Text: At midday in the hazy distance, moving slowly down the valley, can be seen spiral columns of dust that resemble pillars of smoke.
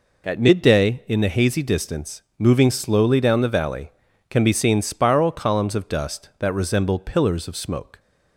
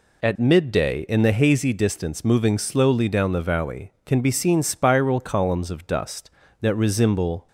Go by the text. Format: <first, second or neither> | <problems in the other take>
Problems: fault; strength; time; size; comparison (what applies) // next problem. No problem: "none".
first | stops before "pillars of smoke"; at 7.4 s